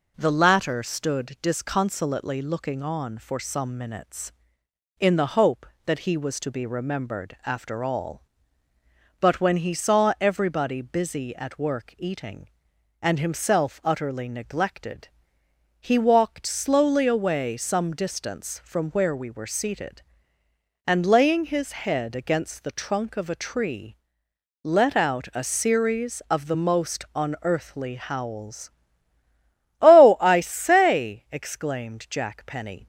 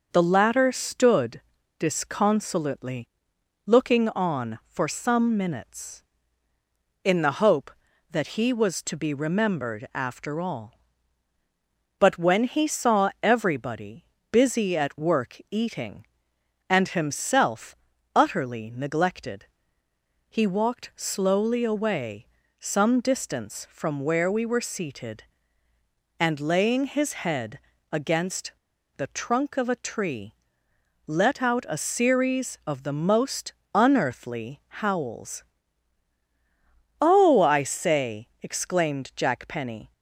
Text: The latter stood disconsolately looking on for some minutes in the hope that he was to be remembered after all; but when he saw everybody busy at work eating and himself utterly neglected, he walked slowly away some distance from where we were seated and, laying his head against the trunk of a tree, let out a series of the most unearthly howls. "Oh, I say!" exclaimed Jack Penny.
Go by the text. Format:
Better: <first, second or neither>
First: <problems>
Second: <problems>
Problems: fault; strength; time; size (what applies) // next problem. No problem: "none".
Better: first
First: none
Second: starts louder than the rest; noticeable; until 1.1 s; 6 dB // pauses between "stood" and "disconsolately"; at 1.3 s; 0.38 s long // pauses between "disconsolately" and "looking"; noticeable; at 3.0 s; 0.58 s long // pauses between "everybody" and "busy"; slight; at 14.0 s; 0.28 s long // pauses between "himself" and "utterly"; at 17.7 s; 0.40 s long // pauses between "away" and "some"; slight; at 22.2 s; 0.34 s long // pauses between "head" and "against"; slight; at 27.5 s; 0.34 s long // pauses between "against" and "the"; at 28.5 s; 0.44 s long // pauses between "most" and "unearthly"; slight; at 33.5 s; 0.20 s long // pauses between "unearthly" and "howls"; slight; at 34.5 s; 0.22 s long